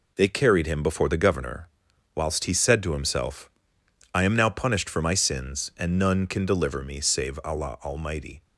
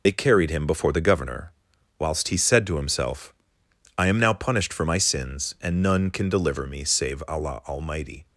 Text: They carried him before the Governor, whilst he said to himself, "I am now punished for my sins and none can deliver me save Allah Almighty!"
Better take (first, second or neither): first